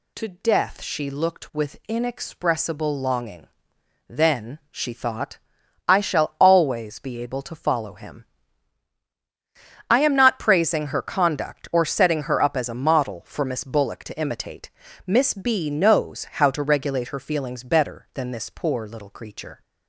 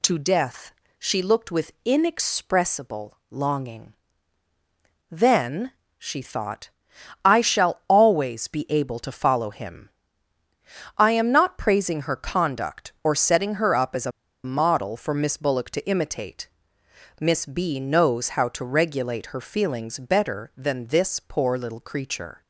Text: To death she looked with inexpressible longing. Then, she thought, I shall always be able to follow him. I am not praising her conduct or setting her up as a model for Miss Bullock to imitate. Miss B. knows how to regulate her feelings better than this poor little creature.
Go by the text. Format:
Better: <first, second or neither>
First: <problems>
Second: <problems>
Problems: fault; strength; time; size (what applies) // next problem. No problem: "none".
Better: first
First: none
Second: pauses between "death" and "she"; slight; at 0.7 s; 0.26 s long // pauses between "a" and "model"; slight; at 14.1 s; 0.33 s long